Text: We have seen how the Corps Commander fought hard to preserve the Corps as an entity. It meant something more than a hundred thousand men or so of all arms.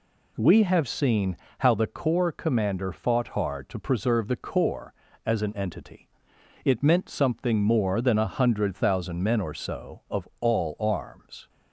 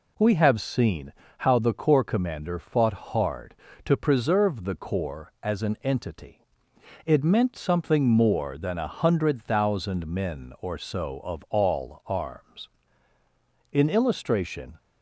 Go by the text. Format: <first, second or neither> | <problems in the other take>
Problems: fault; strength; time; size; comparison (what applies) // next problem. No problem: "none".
first | pauses between "seen" and "how"; slight; at 1.1 s; 0.28 s long; slight in the first // goes on to say "In illustration"; noticeable; from 13.7 s on; 1.0 s long